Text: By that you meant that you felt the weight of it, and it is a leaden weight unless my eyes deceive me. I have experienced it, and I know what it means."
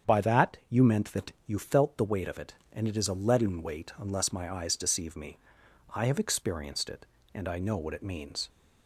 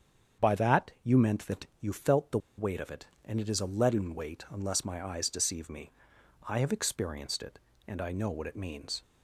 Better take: first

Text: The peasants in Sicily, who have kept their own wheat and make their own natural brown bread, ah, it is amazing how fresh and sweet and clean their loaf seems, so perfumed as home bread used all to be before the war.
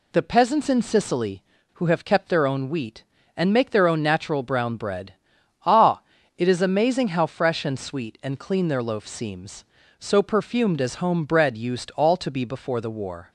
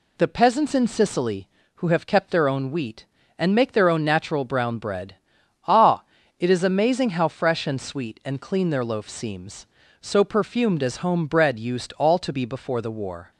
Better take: neither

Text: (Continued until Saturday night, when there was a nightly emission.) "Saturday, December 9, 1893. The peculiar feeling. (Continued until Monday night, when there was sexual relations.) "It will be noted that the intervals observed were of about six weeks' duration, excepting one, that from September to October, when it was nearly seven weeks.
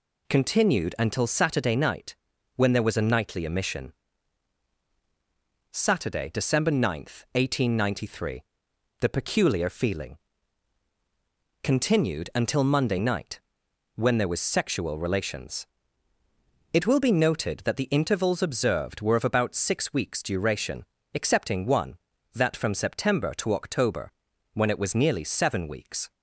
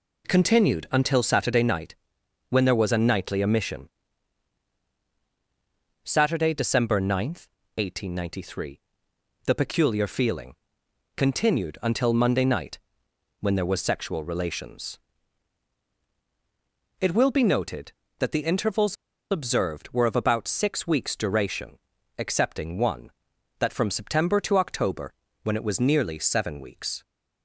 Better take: first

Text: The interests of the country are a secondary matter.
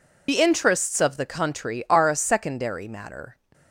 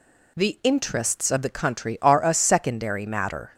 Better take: second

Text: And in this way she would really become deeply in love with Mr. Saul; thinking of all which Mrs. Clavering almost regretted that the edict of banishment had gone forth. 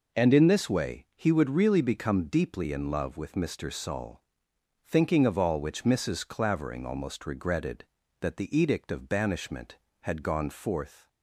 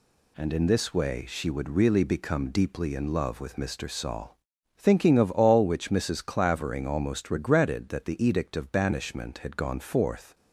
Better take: second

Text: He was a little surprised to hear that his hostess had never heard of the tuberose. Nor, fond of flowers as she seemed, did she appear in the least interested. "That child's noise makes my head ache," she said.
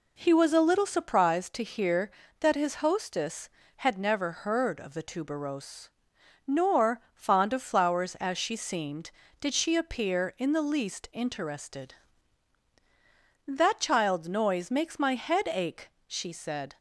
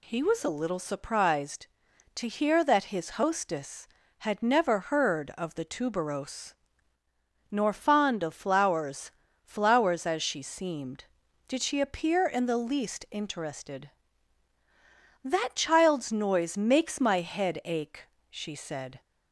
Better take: first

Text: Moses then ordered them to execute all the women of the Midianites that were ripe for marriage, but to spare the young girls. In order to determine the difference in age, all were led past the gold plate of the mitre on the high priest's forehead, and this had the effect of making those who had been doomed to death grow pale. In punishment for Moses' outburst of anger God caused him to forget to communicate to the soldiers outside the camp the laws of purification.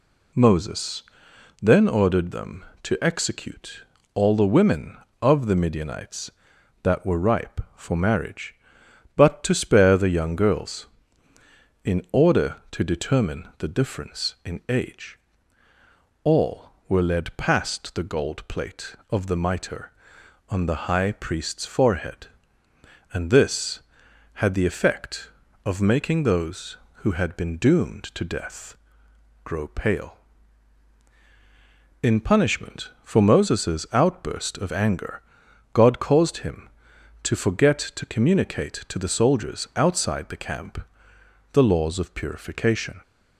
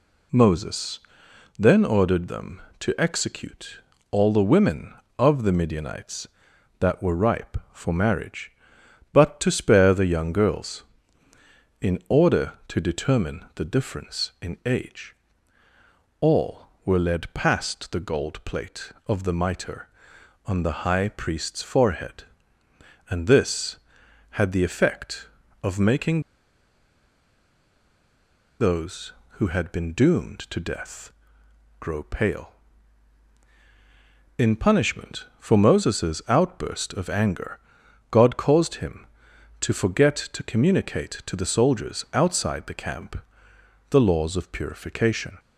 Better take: first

